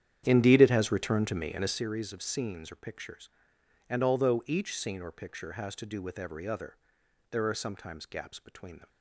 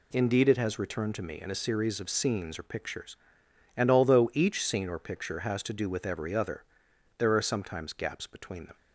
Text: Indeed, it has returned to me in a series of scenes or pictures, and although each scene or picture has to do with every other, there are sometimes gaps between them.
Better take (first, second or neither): second